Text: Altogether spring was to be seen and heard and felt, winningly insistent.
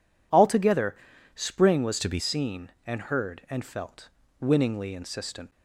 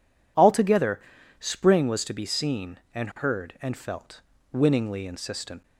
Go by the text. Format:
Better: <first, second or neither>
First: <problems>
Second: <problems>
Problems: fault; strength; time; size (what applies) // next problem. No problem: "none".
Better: second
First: pauses between "Altogether" and "spring"; at 0.9 s; 0.42 s long // changes voice from "to" to "be"; from 1.9 to 2.1 s; 0.2 s long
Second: pauses between "Altogether" and "spring"; at 0.9 s; 0.42 s long